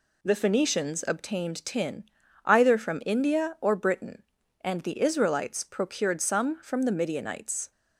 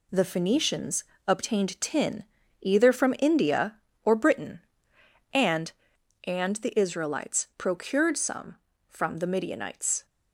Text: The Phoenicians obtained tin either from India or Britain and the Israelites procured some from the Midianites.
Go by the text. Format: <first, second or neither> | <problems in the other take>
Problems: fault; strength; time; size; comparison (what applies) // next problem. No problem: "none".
first | pauses between "Phoenicians" and "obtained"; slight; at 1.0 s; 0.24 s long // pauses between "tin" and "either"; at 2.2 s; 0.38 s long; also in the first // says "and" twice; at 6.2 s